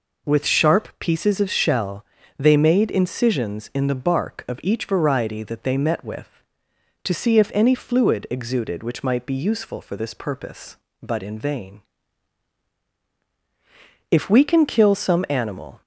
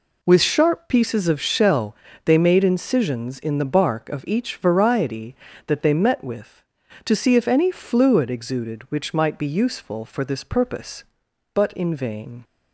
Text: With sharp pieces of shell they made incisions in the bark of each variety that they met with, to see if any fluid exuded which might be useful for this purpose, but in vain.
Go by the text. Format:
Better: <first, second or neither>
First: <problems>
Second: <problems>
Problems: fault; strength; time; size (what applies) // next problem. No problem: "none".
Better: second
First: pauses between "shell" and "they"; slight; at 2.0 s; 0.34 s long // goes on to say "If we can kill some animal"; strong; from 14.0 s on; 1.7 s long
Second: pauses between "shell" and "they"; slight; at 1.9 s; 0.30 s long